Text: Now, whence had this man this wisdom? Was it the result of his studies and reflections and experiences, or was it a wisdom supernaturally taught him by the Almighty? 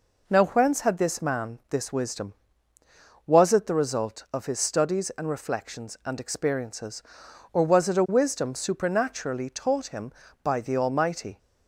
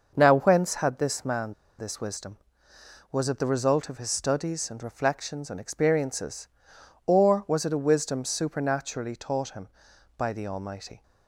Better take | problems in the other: first | starts louder than the rest; noticeable; until 1.1 s; 6 dB // pauses between "man" and "this"; slight; at 1.5 s; 0.24 s long

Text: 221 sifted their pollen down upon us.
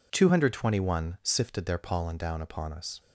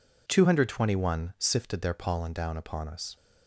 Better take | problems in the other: neither | none

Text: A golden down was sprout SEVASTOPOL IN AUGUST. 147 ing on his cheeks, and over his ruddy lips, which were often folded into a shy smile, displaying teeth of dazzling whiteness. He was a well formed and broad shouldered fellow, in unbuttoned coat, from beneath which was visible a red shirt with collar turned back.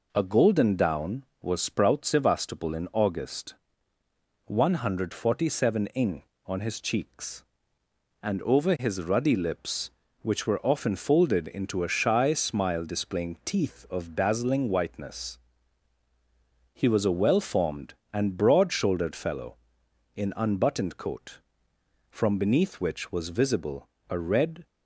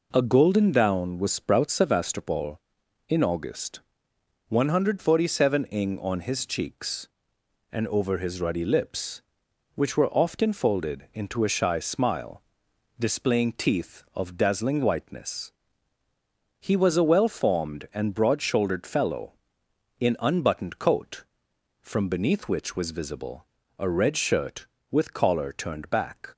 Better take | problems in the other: second | pauses between "visible" and "a"; slight; at 23.8 s; 0.22 s long; slight in the second // stops before "shirt with collar turned back"; at 24.6 s

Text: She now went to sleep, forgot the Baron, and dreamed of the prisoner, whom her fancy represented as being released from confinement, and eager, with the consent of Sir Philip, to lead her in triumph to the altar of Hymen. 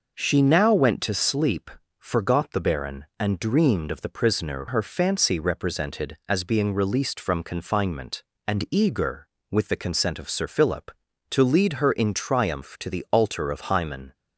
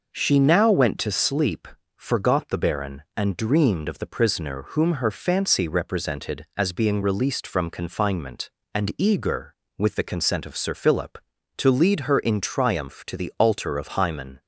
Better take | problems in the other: second | skips "whom"; at 4.6 s

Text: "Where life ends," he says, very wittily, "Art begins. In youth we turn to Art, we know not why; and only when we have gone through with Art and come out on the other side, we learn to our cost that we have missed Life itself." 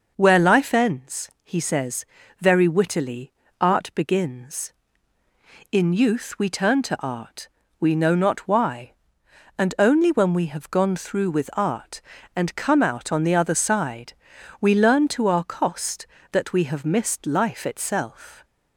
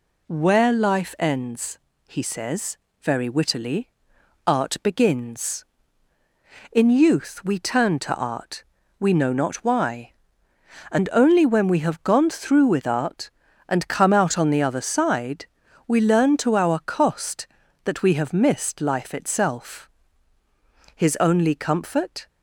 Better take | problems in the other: first | goes on to say "His only comfort"; from 20.9 s on; 1.3 s long

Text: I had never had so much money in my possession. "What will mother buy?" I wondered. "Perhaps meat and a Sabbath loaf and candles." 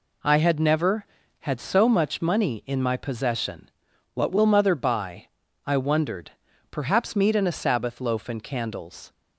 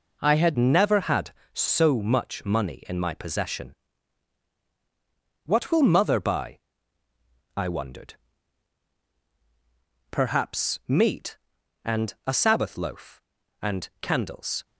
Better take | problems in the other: first | changes voice at "never"; from 0.5 s on; 14.1 s long

